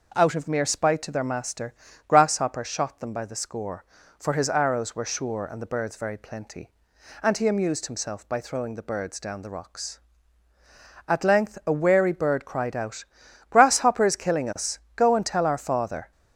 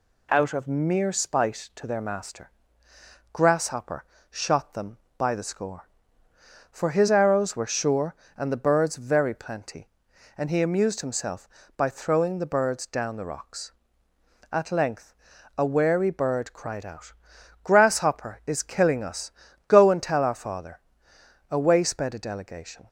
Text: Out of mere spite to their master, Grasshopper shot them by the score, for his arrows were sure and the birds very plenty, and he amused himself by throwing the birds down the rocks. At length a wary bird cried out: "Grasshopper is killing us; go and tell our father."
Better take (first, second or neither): first